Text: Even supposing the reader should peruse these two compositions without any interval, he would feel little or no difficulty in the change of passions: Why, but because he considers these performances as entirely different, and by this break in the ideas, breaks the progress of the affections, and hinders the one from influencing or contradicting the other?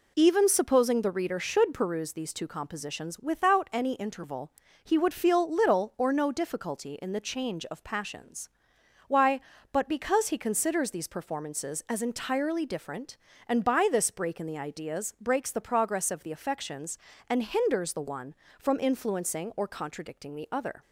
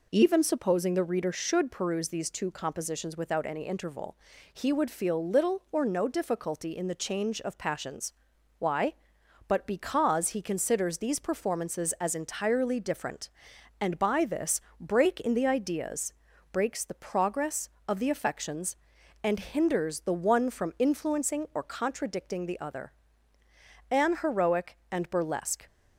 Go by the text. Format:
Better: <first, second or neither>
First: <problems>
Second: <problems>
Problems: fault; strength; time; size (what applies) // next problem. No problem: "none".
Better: first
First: none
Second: pauses between "this" and "break"; slight; at 14.6 s; 0.18 s long // goes on to say "An heroic and burlesque"; strong; from 23.9 s on; 1.7 s long